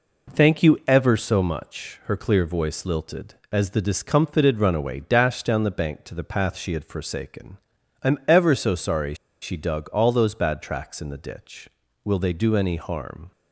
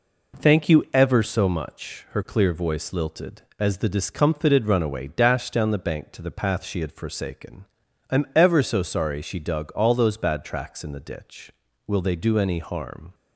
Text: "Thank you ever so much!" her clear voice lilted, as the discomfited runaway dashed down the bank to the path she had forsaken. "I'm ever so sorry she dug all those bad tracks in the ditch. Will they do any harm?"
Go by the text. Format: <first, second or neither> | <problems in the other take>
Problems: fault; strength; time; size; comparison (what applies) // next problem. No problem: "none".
second | pauses between "sorry" and "she"; slight; at 9.1 s; 0.27 s long